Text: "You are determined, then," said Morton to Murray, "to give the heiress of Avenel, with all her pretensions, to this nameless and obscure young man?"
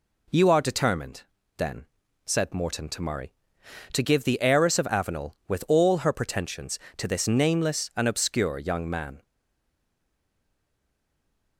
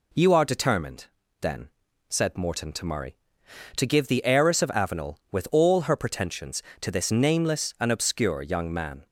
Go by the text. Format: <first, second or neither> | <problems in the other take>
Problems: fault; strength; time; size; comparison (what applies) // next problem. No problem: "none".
second | stays silent after the last word; from 9.2 s on; 2.3 s long